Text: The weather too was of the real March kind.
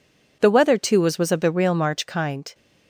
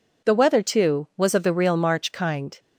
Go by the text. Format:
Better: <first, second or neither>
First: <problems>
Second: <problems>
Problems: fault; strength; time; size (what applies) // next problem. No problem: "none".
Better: second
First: says "was" twice; at 1.1 s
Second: none